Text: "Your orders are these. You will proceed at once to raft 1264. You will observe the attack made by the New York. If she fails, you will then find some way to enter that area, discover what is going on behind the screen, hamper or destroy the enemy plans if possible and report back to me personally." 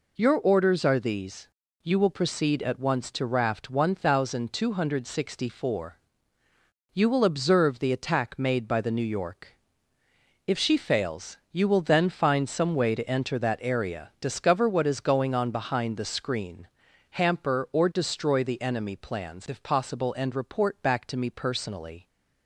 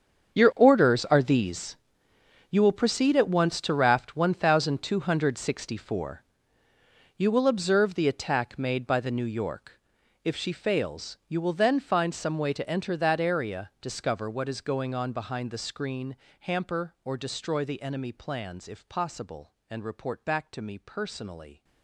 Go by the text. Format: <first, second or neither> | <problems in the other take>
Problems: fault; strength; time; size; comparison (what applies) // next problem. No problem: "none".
first | gets quieter; strong; throughout; 15.5 dB